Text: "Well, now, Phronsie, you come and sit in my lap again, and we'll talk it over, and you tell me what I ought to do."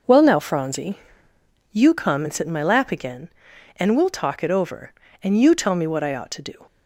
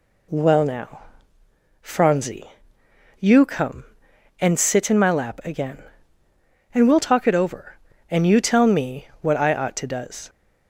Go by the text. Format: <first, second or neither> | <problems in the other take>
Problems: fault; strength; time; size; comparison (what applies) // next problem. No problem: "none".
first | says "does" for "do"; at 9.8 s